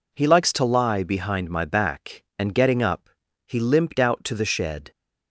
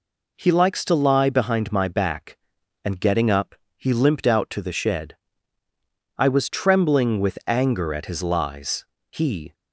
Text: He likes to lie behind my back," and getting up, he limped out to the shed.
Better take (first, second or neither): first